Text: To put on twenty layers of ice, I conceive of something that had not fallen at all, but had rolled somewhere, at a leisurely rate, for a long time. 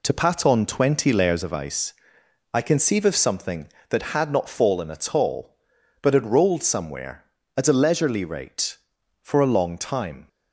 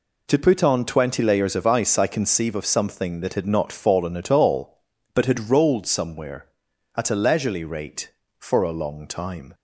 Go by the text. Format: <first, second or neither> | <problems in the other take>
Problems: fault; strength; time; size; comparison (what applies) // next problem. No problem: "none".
second | says "pat" for "put"; at 0.1 s